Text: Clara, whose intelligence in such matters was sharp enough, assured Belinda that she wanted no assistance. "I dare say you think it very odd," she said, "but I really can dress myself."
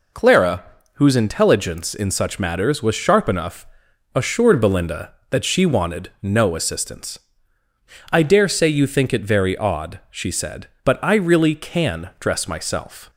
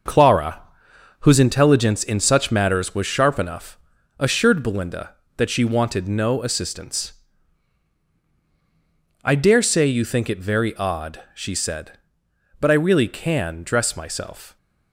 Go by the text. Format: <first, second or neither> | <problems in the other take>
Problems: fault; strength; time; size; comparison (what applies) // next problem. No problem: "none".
first | gets quieter; strong; throughout; 7 dB